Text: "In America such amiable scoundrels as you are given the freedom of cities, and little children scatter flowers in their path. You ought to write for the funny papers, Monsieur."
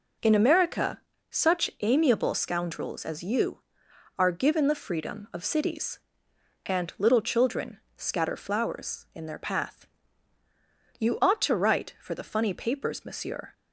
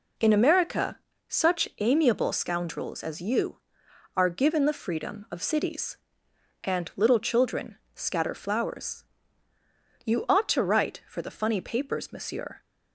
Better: first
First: pauses between "America" and "such"; slight; at 0.9 s; 0.30 s long // pauses between "children" and "scatter"; slight; at 7.7 s; 0.18 s long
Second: pauses between "America" and "such"; slight; at 0.9 s; 0.30 s long // pauses between "children" and "scatter"; slight; at 7.7 s; 0.18 s long // skips "in their path"; at 9.5 s

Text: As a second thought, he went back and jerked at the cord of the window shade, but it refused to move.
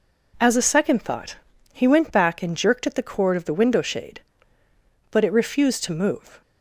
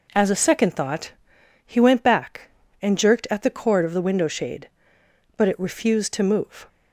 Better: neither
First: none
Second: none

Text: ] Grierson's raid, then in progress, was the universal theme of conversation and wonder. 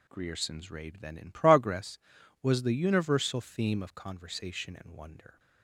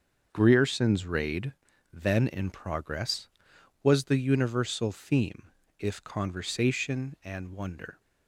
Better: first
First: none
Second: starts louder than the rest; until 1.3 s; 6.5 dB // says "if" for "of"; at 5.7 s

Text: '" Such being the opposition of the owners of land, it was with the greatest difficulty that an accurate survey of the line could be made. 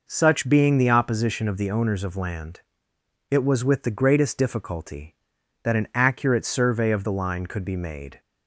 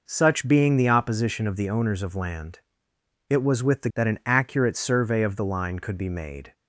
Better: first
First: none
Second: skips "greatest difficulty"; at 3.9 s

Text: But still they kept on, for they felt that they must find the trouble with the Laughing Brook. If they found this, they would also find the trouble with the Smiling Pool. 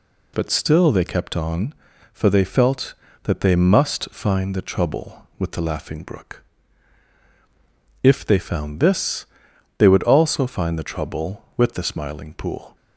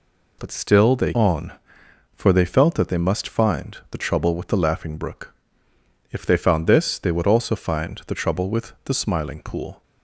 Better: first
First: none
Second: skips "kept"; at 1.1 s

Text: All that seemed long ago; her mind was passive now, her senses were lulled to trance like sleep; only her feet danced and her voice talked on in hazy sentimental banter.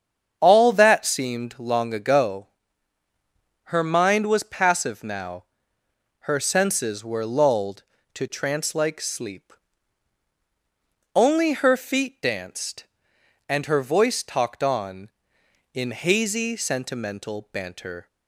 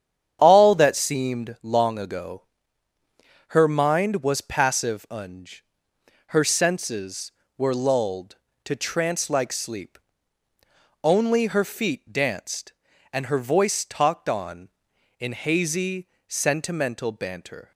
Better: first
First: starts louder than the rest; strong; until 1.4 s; 8 dB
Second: starts louder than the rest; strong; until 1.4 s; 8.5 dB // says "unj" for "now"; at 5.1 s // pauses between "hazy" and "sentimental"; slight; at 16.0 s; 0.18 s long

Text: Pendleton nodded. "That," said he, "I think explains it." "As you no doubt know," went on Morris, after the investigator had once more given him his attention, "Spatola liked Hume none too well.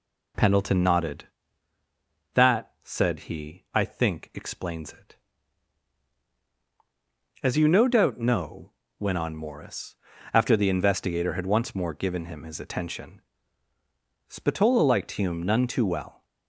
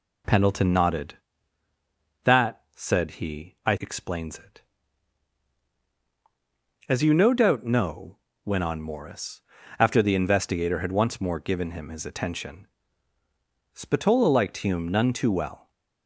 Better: first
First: none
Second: skips "think"; at 3.7 s

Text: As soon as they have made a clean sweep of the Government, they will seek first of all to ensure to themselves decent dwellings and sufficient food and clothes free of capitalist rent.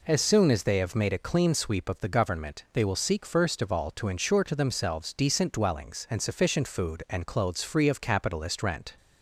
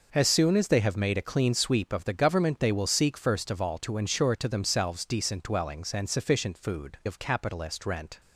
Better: first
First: none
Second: skips "and clothes free"; at 7.0 s

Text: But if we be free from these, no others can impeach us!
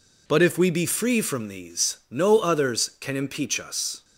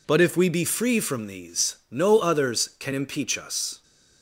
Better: neither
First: none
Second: none

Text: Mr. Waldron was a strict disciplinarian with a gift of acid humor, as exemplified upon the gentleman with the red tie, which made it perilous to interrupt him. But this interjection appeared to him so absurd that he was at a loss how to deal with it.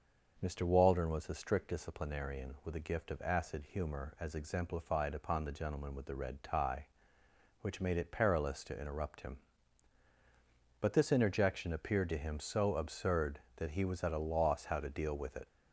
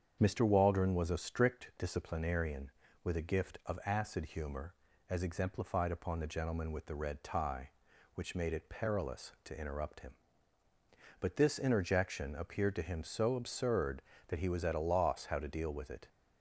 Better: neither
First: starts louder than the rest; noticeable; until 1.4 s; 6 dB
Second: starts louder than the rest; strong; until 1.2 s; 7.5 dB

